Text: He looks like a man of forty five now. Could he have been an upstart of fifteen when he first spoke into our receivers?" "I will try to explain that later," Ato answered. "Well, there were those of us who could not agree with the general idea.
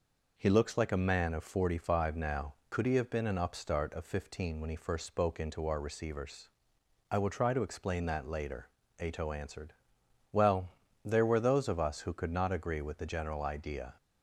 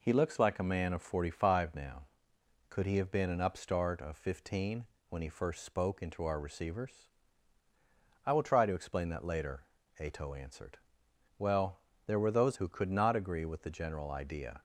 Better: first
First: none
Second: pauses between "fifteen" and "when"; slight; at 4.8 s; 0.24 s long // skips "of us"; at 12.5 s

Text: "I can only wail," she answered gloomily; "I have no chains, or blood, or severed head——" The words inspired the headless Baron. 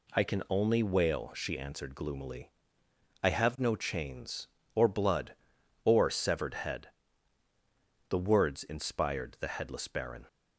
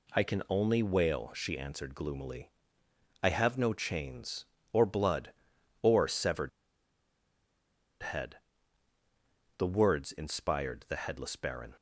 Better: first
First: none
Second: pauses between "severed" and "head"; strong; at 6.4 s; 1.5 s long

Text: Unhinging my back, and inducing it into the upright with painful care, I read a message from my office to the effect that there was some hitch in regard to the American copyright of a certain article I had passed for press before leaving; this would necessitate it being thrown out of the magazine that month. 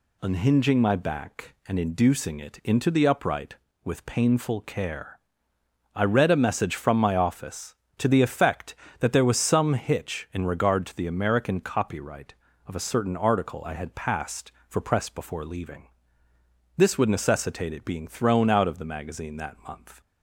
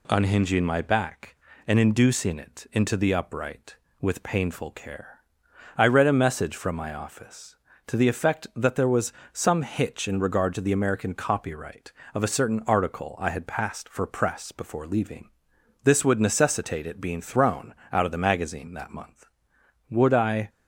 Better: first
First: none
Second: pauses between "was" and "some"; slight; at 9.1 s; 0.20 s long // pauses between "thrown" and "out"; slight; at 17.7 s; 0.16 s long // goes on to say "Would I"; from 19.9 s on; 0.58 s long

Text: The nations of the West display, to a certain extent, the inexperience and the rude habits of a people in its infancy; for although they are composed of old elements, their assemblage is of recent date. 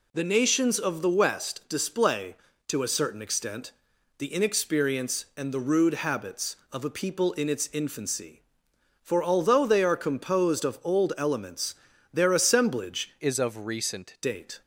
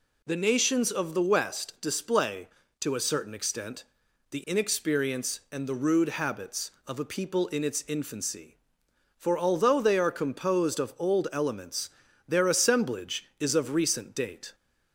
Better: second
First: changes voice from "is" to "recent"; from 13.1 to 14.1 s; 1.0 s long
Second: none

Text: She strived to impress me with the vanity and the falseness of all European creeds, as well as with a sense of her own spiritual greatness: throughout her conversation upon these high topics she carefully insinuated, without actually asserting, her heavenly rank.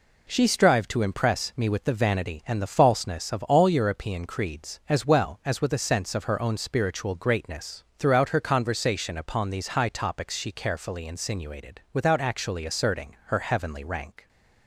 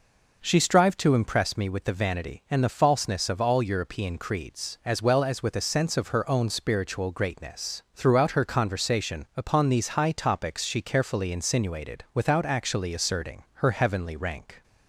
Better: neither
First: none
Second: none

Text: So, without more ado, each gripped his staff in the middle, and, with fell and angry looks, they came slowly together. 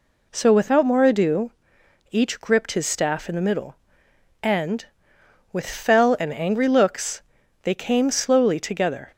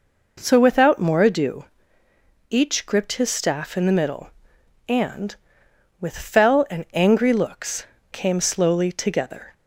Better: first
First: none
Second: skips "they"; at 7.9 s

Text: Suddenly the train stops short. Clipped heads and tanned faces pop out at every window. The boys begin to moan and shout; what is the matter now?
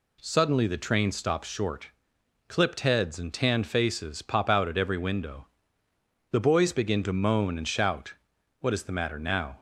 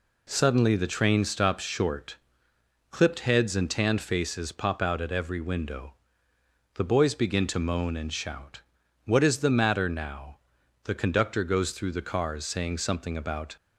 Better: first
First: none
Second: goes on to say "The conductor goes through the cars saying something about"; strong; from 10.8 s on; 2.7 s long

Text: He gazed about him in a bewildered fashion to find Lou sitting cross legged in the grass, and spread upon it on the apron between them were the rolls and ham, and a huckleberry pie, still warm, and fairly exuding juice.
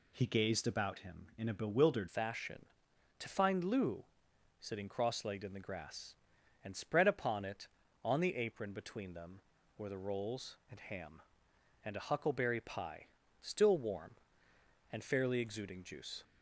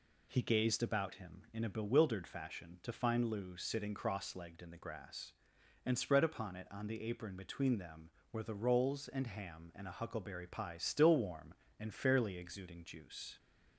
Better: second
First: changes voice at "fashion"; from 2.0 s on; 14.2 s long // pauses between "Lou" and "sitting"; noticeable; at 4.0 s; 0.54 s long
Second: none

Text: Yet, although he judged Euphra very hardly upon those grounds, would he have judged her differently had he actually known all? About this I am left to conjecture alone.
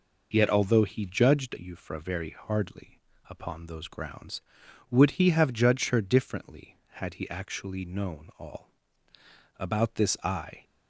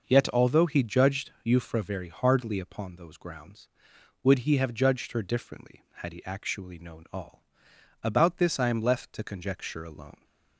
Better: second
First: pauses between "hardly" and "upon"; slight; at 2.9 s; 0.28 s long // stops before "am left to conjecture alone"; at 10.6 s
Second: none

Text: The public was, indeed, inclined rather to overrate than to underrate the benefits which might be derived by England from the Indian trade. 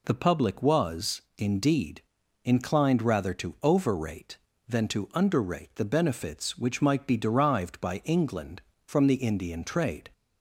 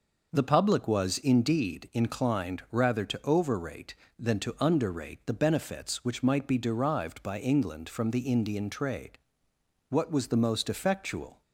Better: first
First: none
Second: goes on to say "What was the most effectual"; from 9.8 s on; 1.5 s long

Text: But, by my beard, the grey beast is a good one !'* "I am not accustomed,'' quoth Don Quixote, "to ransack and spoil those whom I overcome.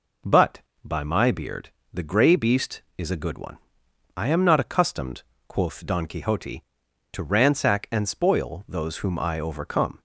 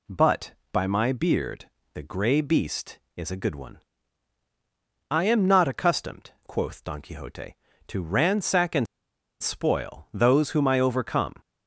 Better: first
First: none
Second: pauses between "and" and "spoil"; noticeable; at 8.8 s; 0.54 s long

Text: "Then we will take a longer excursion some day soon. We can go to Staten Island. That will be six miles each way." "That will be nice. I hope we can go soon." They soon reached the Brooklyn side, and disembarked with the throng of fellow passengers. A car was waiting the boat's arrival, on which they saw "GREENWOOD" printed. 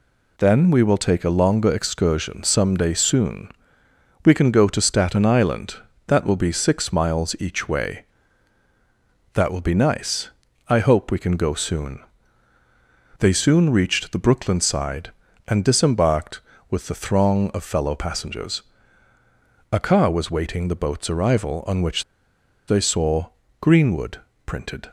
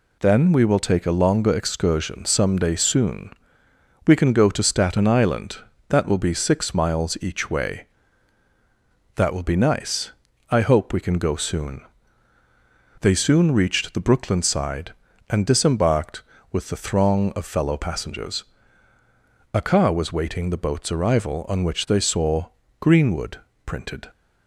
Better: second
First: pauses between "which" and "they"; noticeable; at 22.0 s; 0.65 s long // pauses between "saw" and "GREENWOOD"; slight; at 23.2 s; 0.32 s long // pauses between "GREENWOOD" and "printed"; slight; at 24.1 s; 0.26 s long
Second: pauses between "saw" and "GREENWOOD"; slight; at 22.4 s; 0.32 s long // pauses between "GREENWOOD" and "printed"; slight; at 23.3 s; 0.26 s long

